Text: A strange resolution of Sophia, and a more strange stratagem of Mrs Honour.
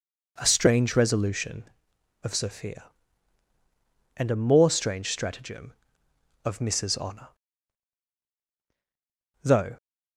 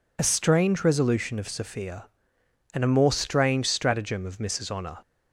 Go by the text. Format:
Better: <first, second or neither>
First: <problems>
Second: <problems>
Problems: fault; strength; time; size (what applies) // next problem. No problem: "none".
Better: second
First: goes on to say "Though"; slight; from 9.4 s on; 0.34 s long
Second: none